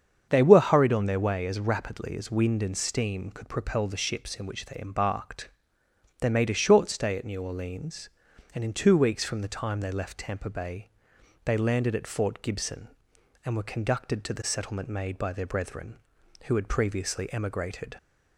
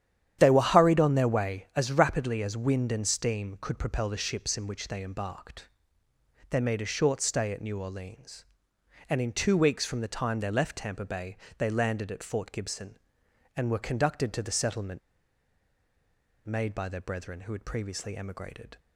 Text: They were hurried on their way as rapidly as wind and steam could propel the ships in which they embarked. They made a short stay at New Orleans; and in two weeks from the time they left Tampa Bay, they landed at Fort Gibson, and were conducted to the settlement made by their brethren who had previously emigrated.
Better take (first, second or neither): first